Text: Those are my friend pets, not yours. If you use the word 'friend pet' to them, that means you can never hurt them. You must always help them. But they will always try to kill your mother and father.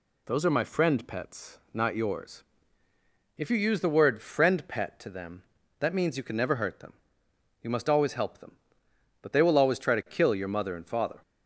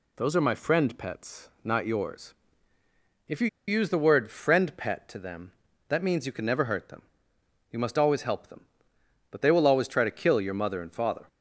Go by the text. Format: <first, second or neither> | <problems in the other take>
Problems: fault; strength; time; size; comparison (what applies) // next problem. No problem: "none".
first | pauses between "you" and "use"; slight; at 3.4 s; 0.20 s long